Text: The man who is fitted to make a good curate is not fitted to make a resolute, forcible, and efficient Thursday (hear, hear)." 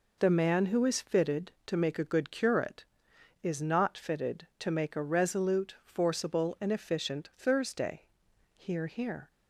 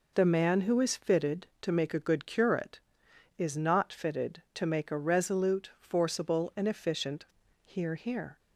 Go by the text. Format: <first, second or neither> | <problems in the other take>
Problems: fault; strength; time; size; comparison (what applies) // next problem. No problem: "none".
first | skips "Thursday"; at 7.4 s